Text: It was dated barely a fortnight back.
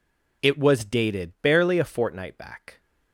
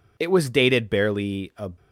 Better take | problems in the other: first | stops before "fortnight back"; at 1.7 s

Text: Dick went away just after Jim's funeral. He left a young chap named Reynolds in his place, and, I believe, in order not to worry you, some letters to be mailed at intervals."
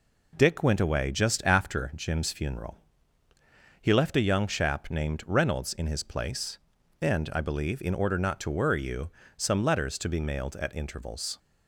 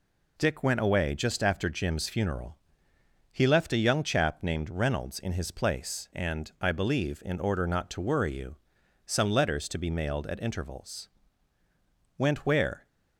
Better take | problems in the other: first | goes on to say "Went where"; noticeable; from 12.1 s on; 0.68 s long

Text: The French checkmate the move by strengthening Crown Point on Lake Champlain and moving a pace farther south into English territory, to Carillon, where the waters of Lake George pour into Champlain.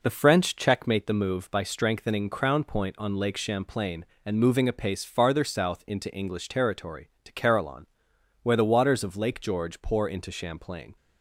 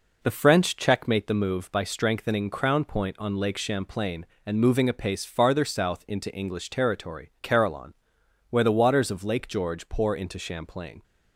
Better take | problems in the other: first | skips "to"; at 7.3 s

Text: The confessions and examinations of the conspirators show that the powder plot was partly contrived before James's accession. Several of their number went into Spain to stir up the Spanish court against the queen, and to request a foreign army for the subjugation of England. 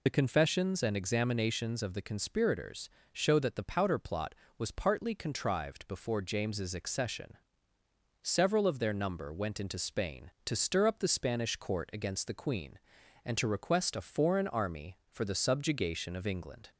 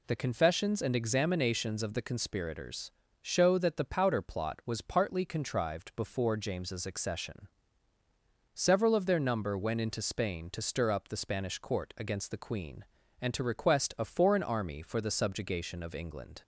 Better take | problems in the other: second | loses the start of "The"; at 0.0 s; 35 ms // pauses between "conspirators" and "show"; slight; at 2.8 s; 0.24 s long; slight in the second

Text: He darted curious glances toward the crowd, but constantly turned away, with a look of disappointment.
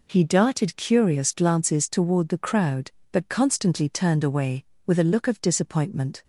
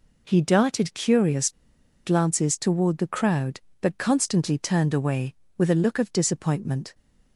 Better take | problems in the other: first | pauses between "curious" and "glances"; noticeable; at 1.5 s; 0.54 s long

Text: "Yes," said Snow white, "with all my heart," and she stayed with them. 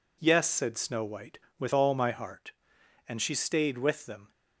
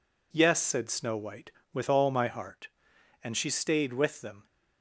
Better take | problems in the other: neither | none

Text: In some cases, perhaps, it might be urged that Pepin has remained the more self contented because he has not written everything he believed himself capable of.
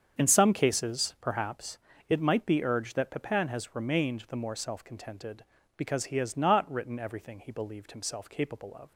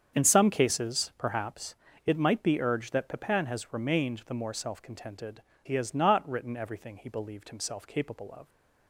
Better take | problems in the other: first | starts louder than the rest; strong; until 1.2 s; 7.5 dB; strong in the first // skips "because"; at 5.5 s

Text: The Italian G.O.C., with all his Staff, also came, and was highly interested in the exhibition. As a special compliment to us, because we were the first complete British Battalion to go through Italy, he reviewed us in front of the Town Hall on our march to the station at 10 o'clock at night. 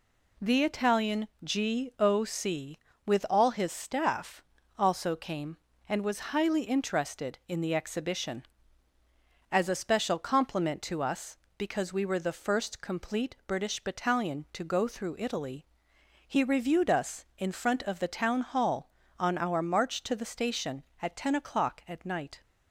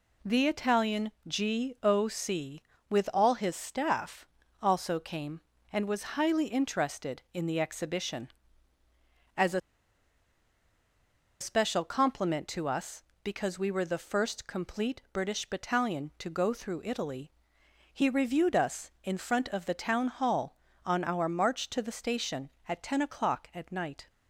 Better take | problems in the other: first | pauses between "a" and "special"; strong; at 9.6 s; 1.8 s long

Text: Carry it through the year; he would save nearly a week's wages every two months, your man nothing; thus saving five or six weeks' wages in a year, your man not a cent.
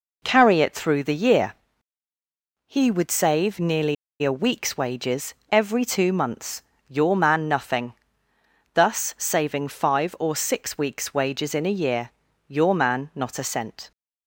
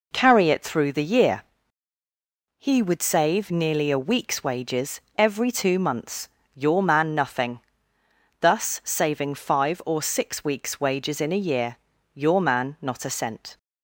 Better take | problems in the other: second | pauses between "nearly" and "a"; slight; at 3.9 s; 0.28 s long // pauses between "wages" and "every"; slight; at 5.3 s; 0.18 s long; slight in the second

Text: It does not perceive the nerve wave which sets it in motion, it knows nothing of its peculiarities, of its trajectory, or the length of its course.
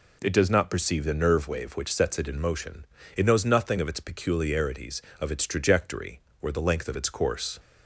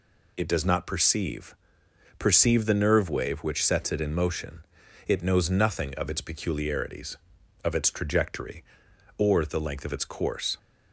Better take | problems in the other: first | says "perceive" twice; at 2.1 s

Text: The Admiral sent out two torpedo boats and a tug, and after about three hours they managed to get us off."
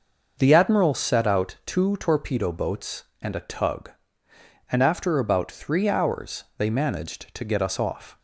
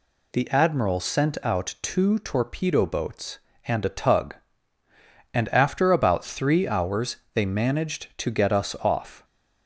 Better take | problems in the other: second | starts louder than the rest; until 1.4 s; 6 dB // says "set" for "sent"; at 0.9 s // pauses between "hours" and "they"; slight; at 6.4 s; 0.16 s long; slight in the second

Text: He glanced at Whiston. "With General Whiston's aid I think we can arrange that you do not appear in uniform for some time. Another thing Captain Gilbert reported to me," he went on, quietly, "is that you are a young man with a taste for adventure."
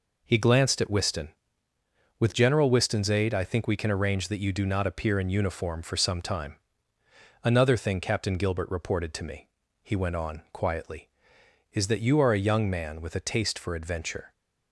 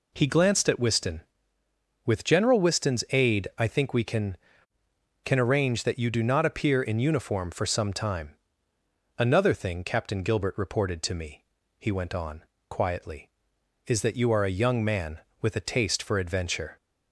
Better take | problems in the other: first | says "can" twice; at 5.2 s

